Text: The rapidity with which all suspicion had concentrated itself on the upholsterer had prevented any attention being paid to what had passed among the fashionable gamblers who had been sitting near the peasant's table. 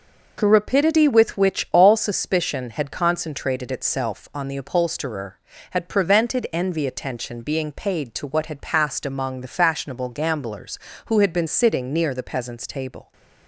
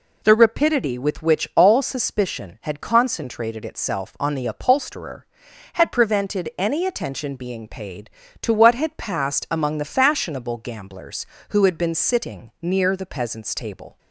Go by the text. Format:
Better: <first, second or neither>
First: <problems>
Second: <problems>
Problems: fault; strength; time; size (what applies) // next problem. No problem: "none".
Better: second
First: says "envy" for "any"; at 6.5 s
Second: none